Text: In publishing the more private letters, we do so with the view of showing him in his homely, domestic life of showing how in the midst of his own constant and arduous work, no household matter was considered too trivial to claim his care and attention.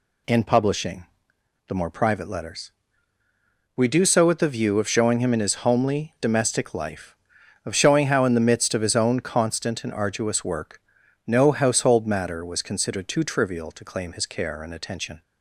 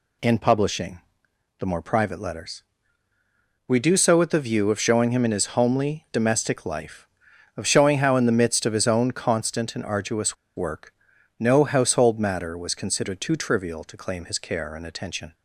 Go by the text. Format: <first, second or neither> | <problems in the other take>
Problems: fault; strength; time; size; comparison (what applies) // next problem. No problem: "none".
first | pauses between "publishing" and "the"; noticeable; at 0.9 s; 0.60 s long; noticeable in the first // pauses between "arduous" and "work"; slight; at 10.3 s; 0.21 s long